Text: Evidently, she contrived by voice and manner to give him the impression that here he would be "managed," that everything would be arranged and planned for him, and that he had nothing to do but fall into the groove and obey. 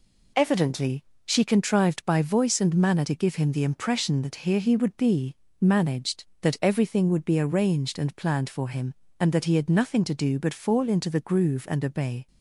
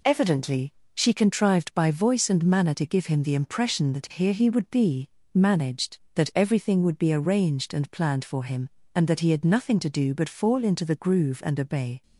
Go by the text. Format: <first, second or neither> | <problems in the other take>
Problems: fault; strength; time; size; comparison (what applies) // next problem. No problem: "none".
neither | pauses between "be" and "managed"; slight; the same in both